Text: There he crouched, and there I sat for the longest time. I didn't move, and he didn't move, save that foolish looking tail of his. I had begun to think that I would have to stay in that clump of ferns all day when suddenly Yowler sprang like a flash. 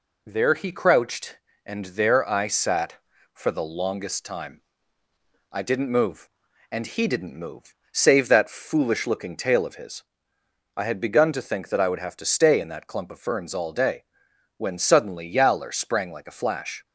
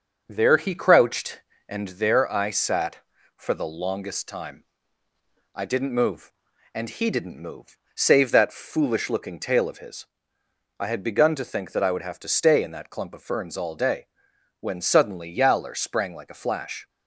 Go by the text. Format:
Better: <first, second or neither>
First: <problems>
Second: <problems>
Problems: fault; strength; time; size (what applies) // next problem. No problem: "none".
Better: first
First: pauses between "day" and "when"; noticeable; at 14.0 s; 0.52 s long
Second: starts louder than the rest; until 1.9 s; 6.5 dB // pauses between "day" and "when"; noticeable; at 14.0 s; 0.52 s long